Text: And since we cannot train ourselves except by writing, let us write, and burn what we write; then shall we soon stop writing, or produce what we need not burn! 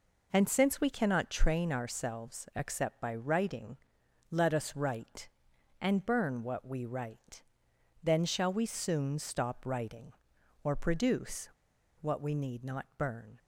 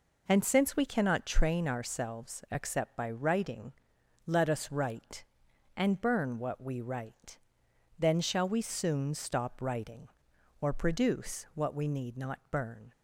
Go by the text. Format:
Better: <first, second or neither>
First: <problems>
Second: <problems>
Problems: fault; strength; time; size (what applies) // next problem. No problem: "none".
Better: second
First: pauses between "produce" and "what"; noticeable; at 11.4 s; 0.52 s long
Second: none